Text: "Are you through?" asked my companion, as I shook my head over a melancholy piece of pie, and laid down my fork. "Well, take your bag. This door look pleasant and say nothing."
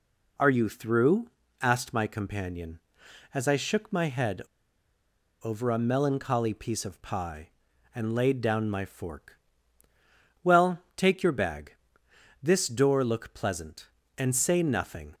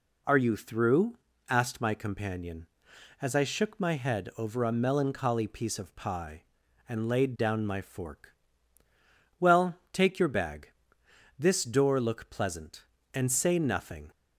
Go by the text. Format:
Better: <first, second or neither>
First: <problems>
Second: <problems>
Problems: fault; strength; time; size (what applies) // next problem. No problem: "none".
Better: second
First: pauses between "head" and "over"; at 4.4 s; 1.0 s long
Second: none